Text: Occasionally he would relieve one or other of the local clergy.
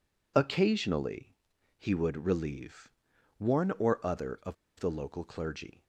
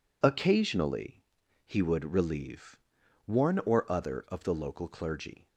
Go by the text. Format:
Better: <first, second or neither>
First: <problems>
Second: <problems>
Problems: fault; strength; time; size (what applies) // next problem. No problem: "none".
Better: second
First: pauses between "Occasionally" and "he"; at 1.3 s; 0.42 s long // pauses between "relieve" and "one"; noticeable; at 2.9 s; 0.46 s long // pauses between "of" and "the"; slight; at 4.5 s; 0.24 s long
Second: pauses between "Occasionally" and "he"; at 1.2 s; 0.42 s long // pauses between "relieve" and "one"; noticeable; at 2.7 s; 0.46 s long